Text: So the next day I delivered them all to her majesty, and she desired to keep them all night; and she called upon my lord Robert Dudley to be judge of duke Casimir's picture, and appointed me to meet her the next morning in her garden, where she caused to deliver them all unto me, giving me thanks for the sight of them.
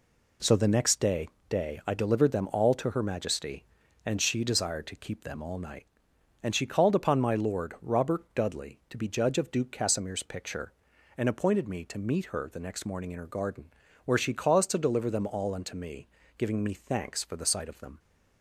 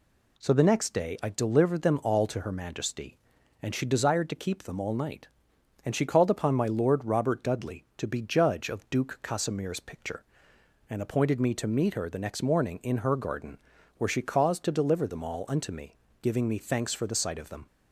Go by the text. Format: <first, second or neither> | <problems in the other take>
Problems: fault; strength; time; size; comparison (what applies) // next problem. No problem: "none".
second | says "day" twice; at 1.4 s